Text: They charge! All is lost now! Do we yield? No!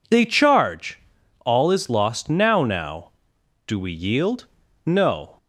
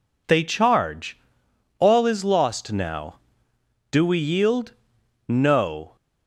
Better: second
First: says "now" twice; at 2.6 s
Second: none

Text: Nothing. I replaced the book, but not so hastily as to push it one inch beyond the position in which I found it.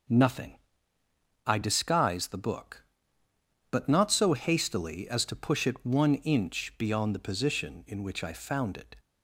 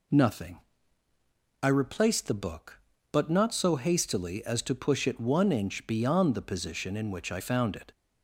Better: second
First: starts louder than the rest; noticeable; until 2.0 s; 6 dB // says "disguise" for "replaced"; at 1.6 s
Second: none

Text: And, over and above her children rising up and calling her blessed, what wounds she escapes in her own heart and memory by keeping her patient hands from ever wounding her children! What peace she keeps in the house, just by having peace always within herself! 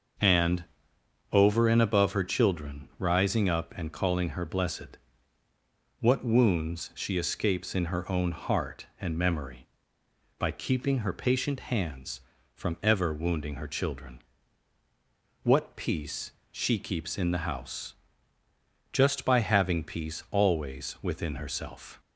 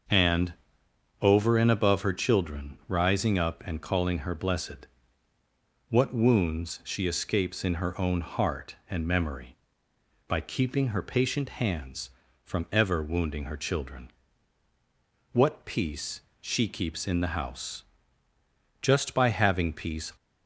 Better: first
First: starts louder than the rest; until 1.8 s; 6.5 dB // pauses between "peace" and "she"; slight; at 16.3 s; 0.18 s long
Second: starts louder than the rest; until 1.7 s; 6.5 dB // pauses between "peace" and "she"; slight; at 16.2 s; 0.18 s long // stops before "always within herself"; at 20.1 s

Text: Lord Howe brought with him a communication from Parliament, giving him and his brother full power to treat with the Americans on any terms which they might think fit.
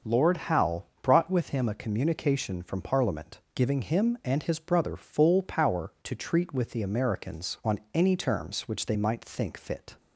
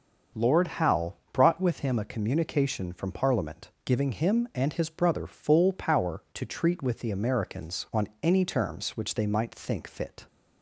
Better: neither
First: starts louder than the rest; until 1.2 s; 6.5 dB // pauses between "Howe" and "brought"; slight; at 0.8 s; 0.18 s long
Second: starts louder than the rest; until 1.5 s; 6.5 dB // pauses between "Howe" and "brought"; slight; at 1.1 s; 0.18 s long

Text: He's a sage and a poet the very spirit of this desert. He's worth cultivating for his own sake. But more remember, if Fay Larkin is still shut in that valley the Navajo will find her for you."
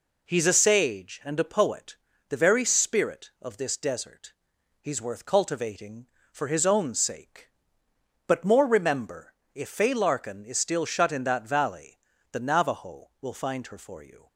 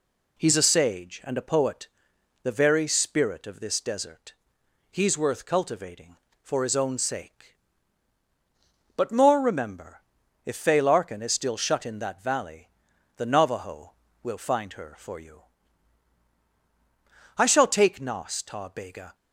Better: first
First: pauses between "poet" and "the"; slight; at 1.9 s; 0.32 s long // pauses between "valley" and "the"; slight; at 11.9 s; 0.36 s long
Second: pauses between "poet" and "the"; noticeable; at 1.8 s; 0.54 s long // pauses between "valley" and "the"; noticeable; at 12.6 s; 0.48 s long // goes on to say "I shall take Nas Ta Bega"; strong; from 17.3 s on; 1.7 s long

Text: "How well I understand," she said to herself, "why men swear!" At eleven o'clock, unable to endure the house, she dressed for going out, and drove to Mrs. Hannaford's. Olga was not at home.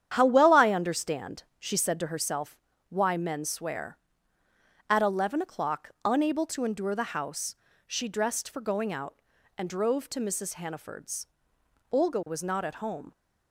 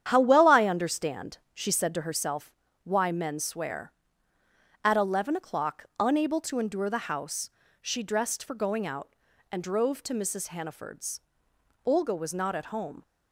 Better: neither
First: starts louder than the rest; strong; until 1.1 s; 9.5 dB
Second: starts louder than the rest; strong; until 1.1 s; 9.5 dB

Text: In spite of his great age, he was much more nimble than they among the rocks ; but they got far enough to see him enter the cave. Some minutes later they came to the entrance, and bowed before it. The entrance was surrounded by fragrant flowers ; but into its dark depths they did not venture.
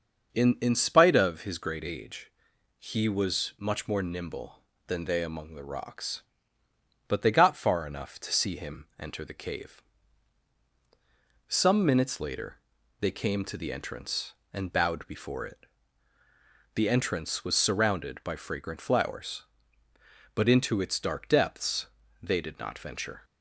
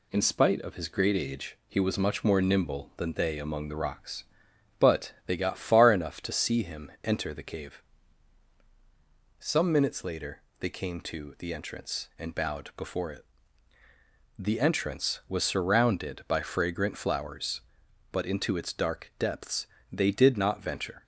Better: second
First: starts louder than the rest; until 1.3 s; 6.5 dB // says "In" twice; at 0.6 s // pauses between "later" and "they"; at 12.6 s; 0.40 s long // pauses between "depths" and "they"; slight; at 21.8 s; 0.34 s long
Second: pauses between "later" and "they"; slight; at 10.4 s; 0.20 s long // pauses between "depths" and "they"; slight; at 19.6 s; 0.24 s long

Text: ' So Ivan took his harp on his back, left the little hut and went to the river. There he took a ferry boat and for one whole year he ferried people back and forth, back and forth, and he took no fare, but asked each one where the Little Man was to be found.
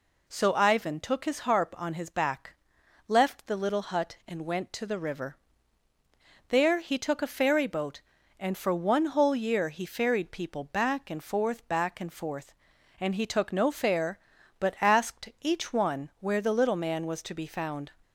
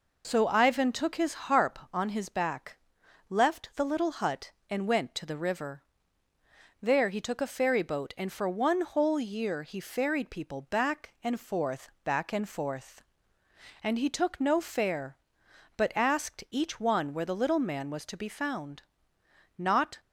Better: first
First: none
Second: goes on to say "Not"; slight; from 19.5 s on; 0.44 s long

